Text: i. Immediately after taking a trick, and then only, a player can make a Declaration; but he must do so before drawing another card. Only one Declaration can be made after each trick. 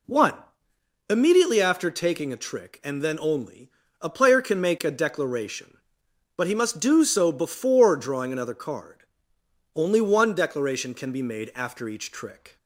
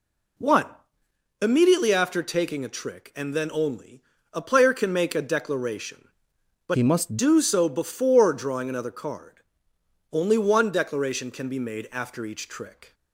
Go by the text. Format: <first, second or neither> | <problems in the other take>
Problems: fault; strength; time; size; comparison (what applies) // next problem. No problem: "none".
first | changes voice from "he" to "must"; from 6.7 to 7.1 s; 0.4 s long